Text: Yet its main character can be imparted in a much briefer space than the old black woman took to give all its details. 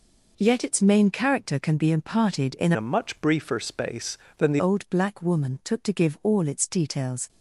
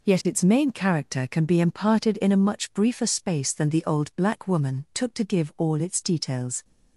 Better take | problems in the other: second | changes voice from "a" to "the"; from 2.7 to 4.5 s; 1.8 s long

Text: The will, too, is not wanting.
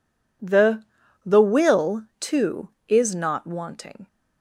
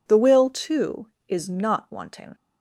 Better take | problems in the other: second | says "The" twice; at 1.2 s

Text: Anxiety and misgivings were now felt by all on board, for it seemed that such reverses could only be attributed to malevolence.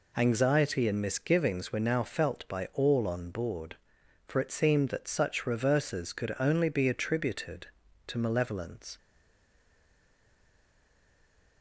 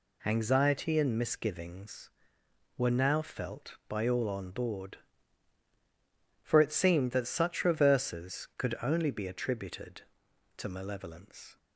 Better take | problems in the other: second | stays silent after the last word; strong; from 8.9 s on; 2.7 s long

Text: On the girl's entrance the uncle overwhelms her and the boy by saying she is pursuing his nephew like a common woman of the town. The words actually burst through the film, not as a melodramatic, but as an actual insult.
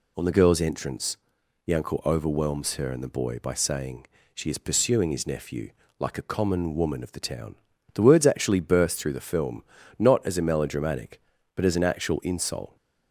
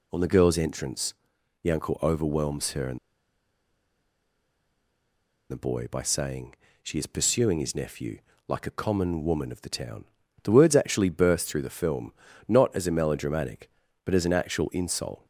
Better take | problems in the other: first | pauses between "entrance" and "the"; noticeable; at 1.1 s; 0.48 s long; noticeable in the first // pauses between "and" and "the"; strong; at 2.9 s; 2.5 s long // pauses between "saying" and "she"; slight; at 6.5 s; 0.30 s long; slight in the first // pauses between "nephew" and "like"; slight; at 8.1 s; 0.26 s long; slight in the first

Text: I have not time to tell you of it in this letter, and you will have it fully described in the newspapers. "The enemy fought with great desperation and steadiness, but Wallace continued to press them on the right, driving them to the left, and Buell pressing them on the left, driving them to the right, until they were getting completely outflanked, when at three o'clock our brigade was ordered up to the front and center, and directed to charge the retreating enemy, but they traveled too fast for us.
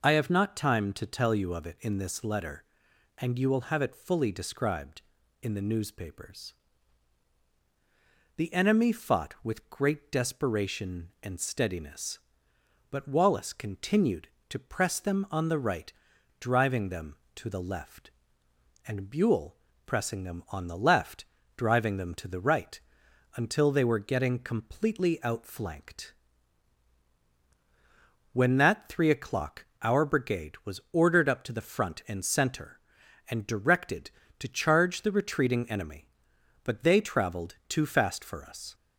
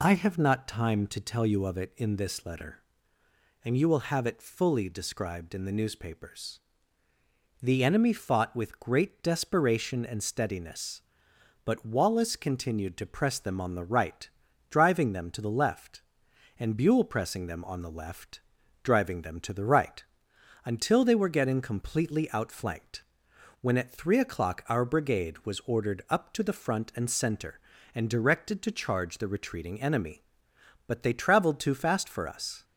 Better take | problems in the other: second | pauses between "Buell" and "pressing"; slight; at 19.5 s; 0.30 s long // says "that" for "at"; at 28.5 s // pauses between "o'clock" and "our"; slight; at 29.6 s; 0.16 s long

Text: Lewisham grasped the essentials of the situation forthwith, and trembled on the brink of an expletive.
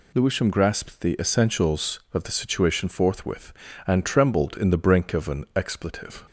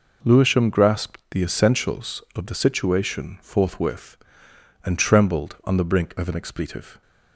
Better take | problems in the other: second | says "in" for "on"; at 4.5 s

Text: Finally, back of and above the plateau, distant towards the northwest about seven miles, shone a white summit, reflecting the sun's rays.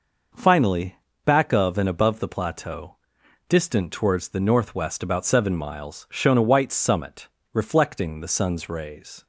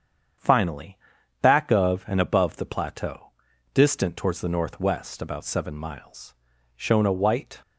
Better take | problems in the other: first | starts louder than the rest; strong; until 1.8 s; 7.5 dB // stops before "summit reflecting the sun's rays"; at 7.6 s

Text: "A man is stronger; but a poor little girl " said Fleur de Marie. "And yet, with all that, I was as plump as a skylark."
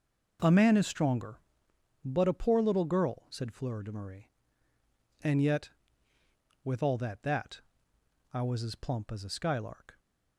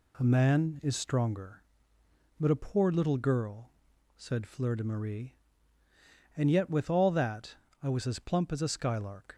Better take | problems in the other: second | says "that" twice; at 7.2 s

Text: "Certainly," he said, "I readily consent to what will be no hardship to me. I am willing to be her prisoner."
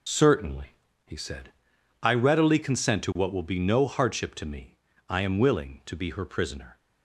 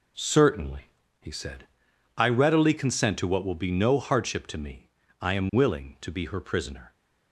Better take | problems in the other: second | loses the start of "Certainly"; at 0.0 s; 50 ms

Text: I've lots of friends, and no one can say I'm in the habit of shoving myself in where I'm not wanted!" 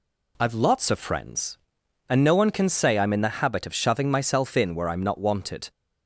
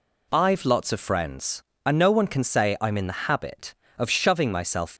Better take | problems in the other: first | stops before "in where I'm not wanted"; at 4.9 s

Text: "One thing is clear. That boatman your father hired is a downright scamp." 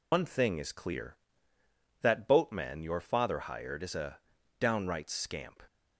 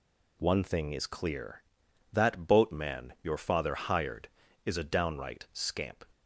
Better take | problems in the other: second | loses the start of "One"; at 0.1 s; 100 ms // pauses between "a" and "downright"; at 4.1 s; 0.40 s long

